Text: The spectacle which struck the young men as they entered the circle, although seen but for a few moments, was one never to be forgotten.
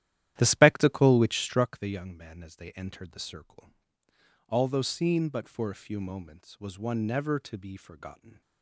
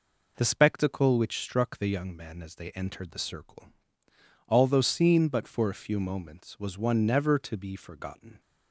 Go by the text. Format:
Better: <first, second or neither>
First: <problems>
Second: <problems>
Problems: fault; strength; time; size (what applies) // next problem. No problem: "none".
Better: second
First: starts louder than the rest; strong; until 1.8 s; 12.5 dB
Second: none